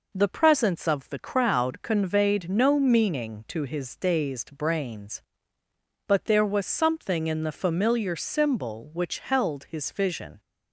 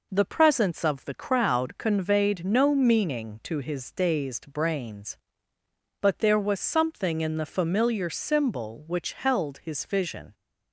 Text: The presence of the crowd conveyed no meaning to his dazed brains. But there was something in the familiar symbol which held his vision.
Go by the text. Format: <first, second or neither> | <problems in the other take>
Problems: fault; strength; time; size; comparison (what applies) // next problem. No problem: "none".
neither | none